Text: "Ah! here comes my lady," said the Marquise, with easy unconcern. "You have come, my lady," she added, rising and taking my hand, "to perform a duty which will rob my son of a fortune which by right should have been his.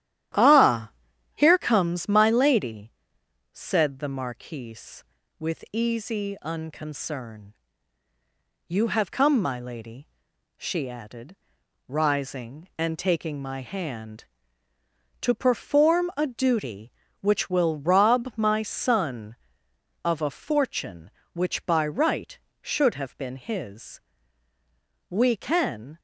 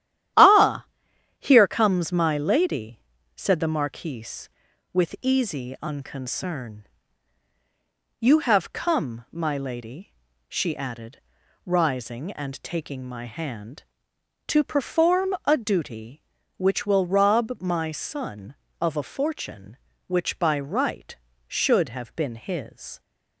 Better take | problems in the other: second | starts louder than the rest; strong; until 1.8 s; 12.5 dB; strong in the second // goes on to say "We can"; noticeable; from 25.1 s on; 0.88 s long

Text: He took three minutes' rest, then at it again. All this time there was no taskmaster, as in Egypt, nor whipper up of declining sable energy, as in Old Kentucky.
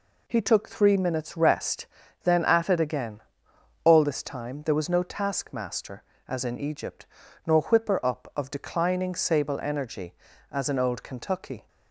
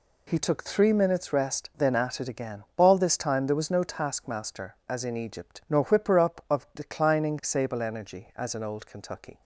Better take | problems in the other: neither | none

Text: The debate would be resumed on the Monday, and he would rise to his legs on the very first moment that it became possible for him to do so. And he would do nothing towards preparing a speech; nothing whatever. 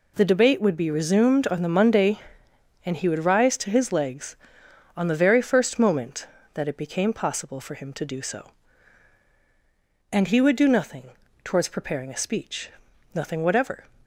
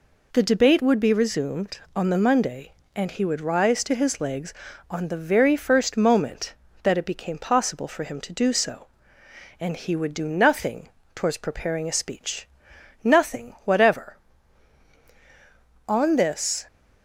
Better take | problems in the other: first | pauses between "nothing" and "towards"; slight; at 10.8 s; 0.26 s long; slight in the first // goes on to say "On this"; noticeable; from 15.8 s on; 0.78 s long

